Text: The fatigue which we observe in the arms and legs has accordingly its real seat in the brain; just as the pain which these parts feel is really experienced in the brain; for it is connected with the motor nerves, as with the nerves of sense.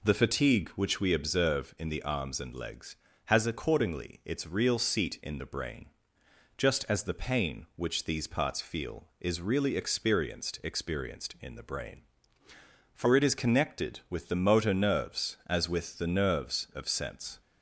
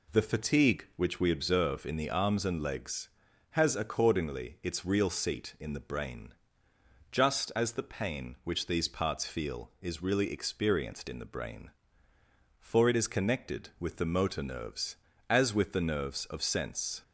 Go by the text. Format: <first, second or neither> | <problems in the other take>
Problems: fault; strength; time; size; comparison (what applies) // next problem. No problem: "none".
second | says "experienced" twice; at 10.6 s